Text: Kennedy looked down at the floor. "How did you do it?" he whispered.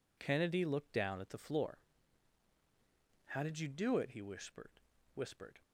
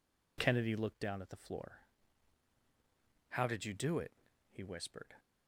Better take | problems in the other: second | says "whispered" twice; at 5.1 s

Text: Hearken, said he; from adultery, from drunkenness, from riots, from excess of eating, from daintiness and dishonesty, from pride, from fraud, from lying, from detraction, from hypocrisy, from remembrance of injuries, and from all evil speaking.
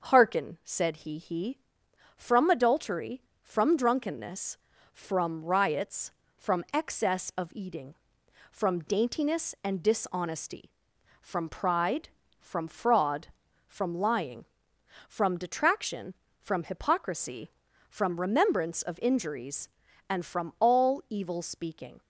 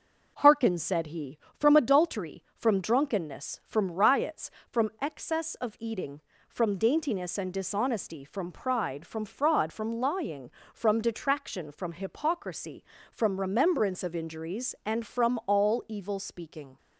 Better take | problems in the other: second | says "he" twice; at 1.1 s

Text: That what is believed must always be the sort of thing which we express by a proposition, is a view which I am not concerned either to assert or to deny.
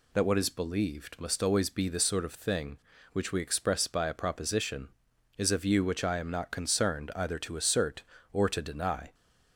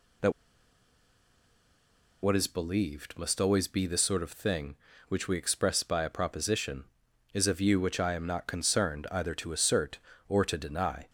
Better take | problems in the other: first | pauses between "That" and "what"; strong; at 0.3 s; 1.9 s long

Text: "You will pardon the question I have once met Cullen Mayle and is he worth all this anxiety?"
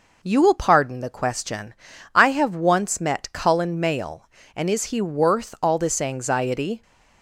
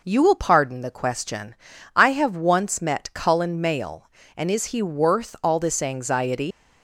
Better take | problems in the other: first | pauses between "question" and "I"; at 1.5 s; 0.40 s long; also in the first // leaves "anxiety" unfinished; at 6.5 s; 120 ms

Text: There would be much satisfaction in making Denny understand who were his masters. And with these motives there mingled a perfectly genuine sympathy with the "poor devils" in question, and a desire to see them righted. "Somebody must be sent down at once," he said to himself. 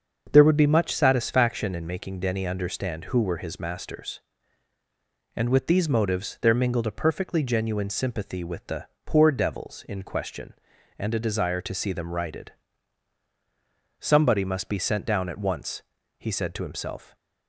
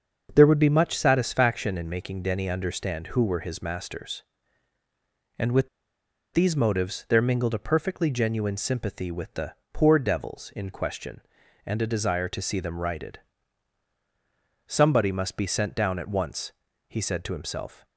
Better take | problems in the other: first | starts louder than the rest; until 1.3 s; 6.5 dB; also in the first // pauses between "with" and "these"; noticeable; at 5.6 s; 0.66 s long // pauses between "the" and "poor"; slight; at 9.5 s; 0.18 s long; slight in the first

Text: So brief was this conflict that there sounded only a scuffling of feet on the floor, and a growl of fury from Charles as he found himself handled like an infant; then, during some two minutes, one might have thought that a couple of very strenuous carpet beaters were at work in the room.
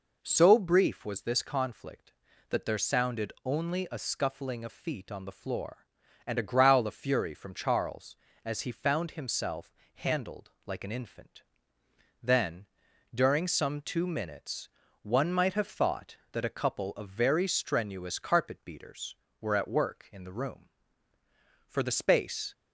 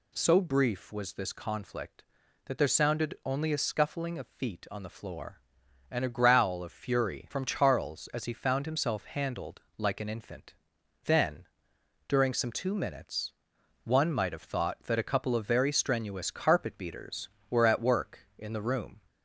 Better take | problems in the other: second | pauses between "himself" and "handled"; slight; at 9.7 s; 0.22 s long // pauses between "handled" and "like"; slight; at 10.5 s; 0.16 s long; slight in the second // goes on to say "For the space"; noticeable; from 21.6 s on; 0.86 s long

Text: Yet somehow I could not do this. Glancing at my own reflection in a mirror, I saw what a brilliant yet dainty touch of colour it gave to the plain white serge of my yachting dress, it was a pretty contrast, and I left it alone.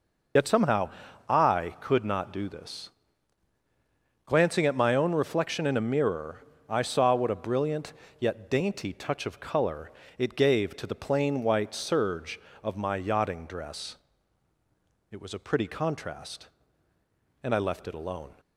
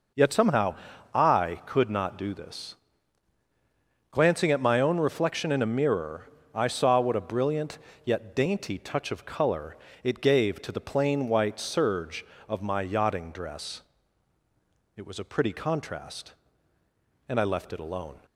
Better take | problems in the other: second | loses the start of "Yet"; at 0.3 s; 55 ms // pauses between "somehow" and "I"; at 0.8 s; 0.38 s long; also in the second // pauses between "brilliant" and "yet"; slight; at 7.9 s; 0.24 s long; slight in the second // pauses between "colour" and "it"; slight; at 9.9 s; 0.26 s long; slight in the second

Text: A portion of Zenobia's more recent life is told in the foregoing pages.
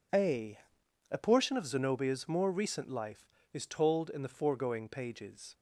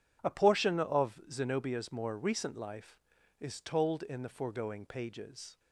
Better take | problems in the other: second | says "A" twice; at 1.1 s

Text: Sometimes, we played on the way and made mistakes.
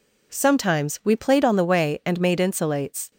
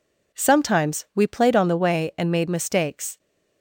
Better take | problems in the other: second | says "insulates" for "mistakes"; at 2.3 s

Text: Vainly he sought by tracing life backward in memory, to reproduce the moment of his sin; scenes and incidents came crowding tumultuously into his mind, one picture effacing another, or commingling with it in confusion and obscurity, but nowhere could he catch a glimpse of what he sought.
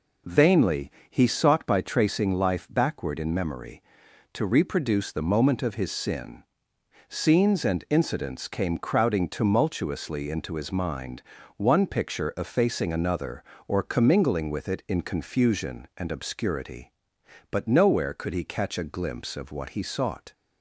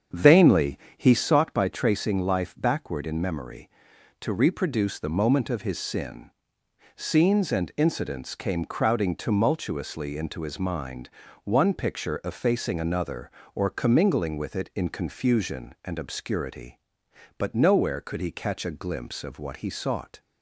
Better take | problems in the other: first | starts louder than the rest; strong; until 1.4 s; 7.5 dB // pauses between "Vainly" and "he"; slight; at 0.7 s; 0.20 s long; slight in the first

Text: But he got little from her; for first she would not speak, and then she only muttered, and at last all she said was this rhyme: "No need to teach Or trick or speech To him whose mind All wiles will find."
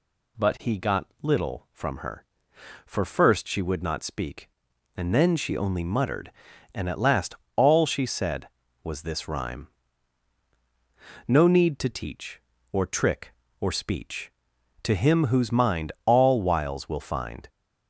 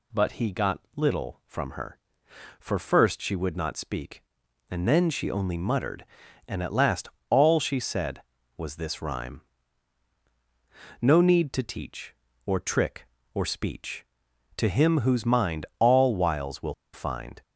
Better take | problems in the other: first | pauses between "got" and "little"; slight; at 0.8 s; 0.16 s long; slight in the first // pauses between "last" and "all"; slight; at 7.0 s; 0.20 s long; slight in the first // pauses between "will" and "find"; slight; at 16.7 s; 0.19 s long

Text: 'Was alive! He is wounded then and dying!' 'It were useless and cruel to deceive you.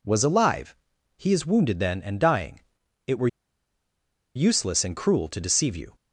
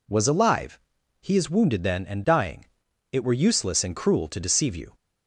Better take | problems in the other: second | pauses between "were" and "useless"; at 3.2 s; 1.0 s long

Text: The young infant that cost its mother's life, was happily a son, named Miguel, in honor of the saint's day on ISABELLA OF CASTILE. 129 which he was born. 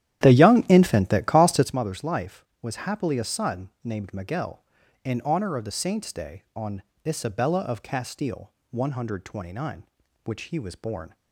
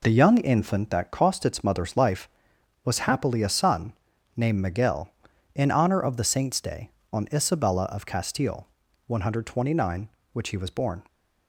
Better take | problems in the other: second | starts louder than the rest; strong; until 1.7 s; 11.5 dB // pauses between "on" and "ISABELLA"; slight; at 6.8 s; 0.24 s long

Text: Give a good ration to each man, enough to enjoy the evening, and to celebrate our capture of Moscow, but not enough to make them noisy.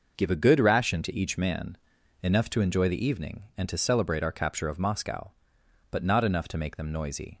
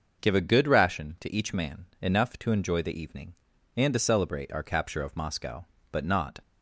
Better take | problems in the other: first | starts louder than the rest; until 1.2 s; 6.5 dB // stops before "enough to make them noisy"; at 6.4 s

